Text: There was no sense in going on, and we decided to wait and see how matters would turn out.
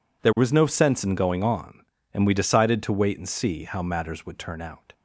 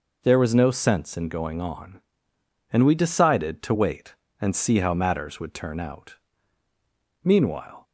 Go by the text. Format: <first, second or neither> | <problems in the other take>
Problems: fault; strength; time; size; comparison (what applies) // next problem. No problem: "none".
first | goes on to say "Meanwhile"; from 7.2 s on; 0.60 s long